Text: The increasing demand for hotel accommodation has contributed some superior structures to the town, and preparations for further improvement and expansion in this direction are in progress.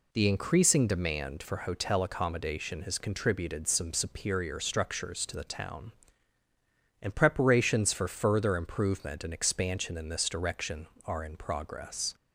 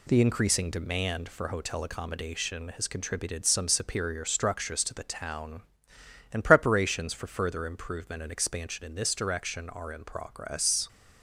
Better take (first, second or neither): neither